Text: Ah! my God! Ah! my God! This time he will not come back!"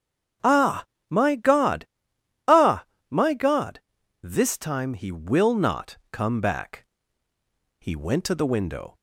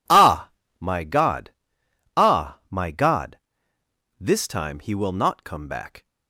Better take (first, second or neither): second